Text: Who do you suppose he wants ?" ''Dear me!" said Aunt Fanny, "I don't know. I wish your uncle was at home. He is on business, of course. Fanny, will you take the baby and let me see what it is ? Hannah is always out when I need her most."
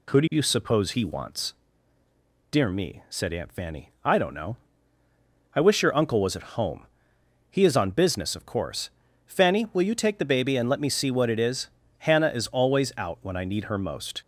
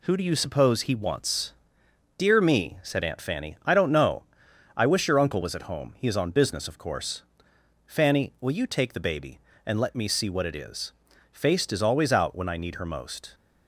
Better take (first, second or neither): first